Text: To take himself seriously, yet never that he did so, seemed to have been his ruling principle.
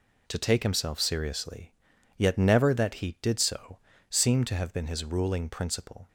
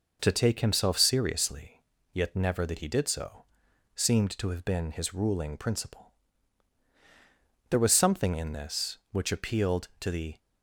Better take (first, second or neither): first